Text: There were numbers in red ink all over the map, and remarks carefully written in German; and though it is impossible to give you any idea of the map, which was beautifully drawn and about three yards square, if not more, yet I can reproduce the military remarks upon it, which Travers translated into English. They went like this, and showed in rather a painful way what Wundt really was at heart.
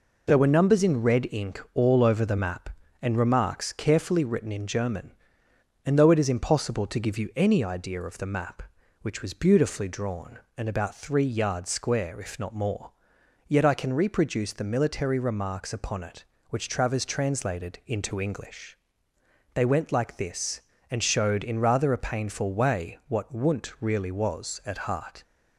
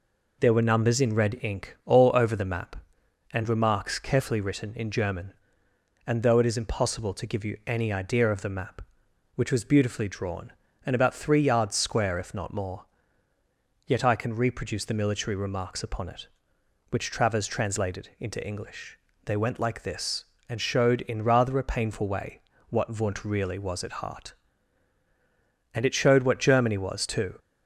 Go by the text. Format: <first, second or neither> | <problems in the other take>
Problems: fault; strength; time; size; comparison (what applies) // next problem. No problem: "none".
first | pauses between "way" and "what"; slight; at 22.4 s; 0.28 s long // goes on to say "And it showed what Germany was too"; from 25.7 s on; 1.6 s long